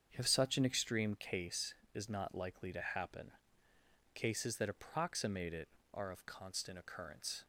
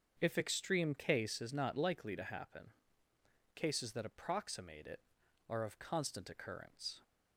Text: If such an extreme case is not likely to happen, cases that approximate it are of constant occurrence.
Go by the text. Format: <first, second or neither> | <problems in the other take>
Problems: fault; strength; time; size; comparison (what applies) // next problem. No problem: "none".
first | starts louder than the rest; until 1.2 s; 7 dB; also in the first // skips "such an"; at 0.3 s